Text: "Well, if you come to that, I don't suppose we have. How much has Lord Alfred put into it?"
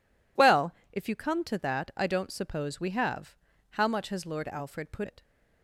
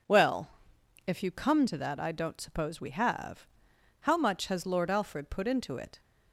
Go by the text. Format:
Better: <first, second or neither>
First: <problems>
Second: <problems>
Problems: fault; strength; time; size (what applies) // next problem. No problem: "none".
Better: second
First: skips "into"; at 5.0 s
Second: none